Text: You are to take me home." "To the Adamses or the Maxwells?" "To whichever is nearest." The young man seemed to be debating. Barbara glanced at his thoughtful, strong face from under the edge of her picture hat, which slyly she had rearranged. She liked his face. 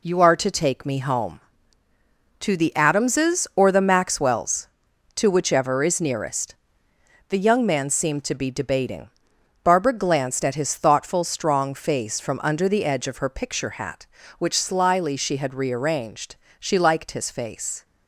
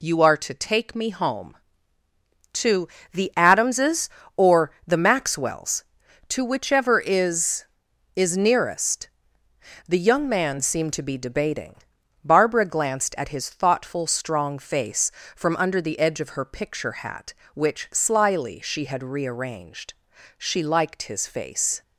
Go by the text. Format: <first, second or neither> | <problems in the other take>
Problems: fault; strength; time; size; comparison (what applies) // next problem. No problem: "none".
first | pauses between "To" and "the"; slight; at 2.8 s; 0.24 s long // says "is" twice; at 8.1 s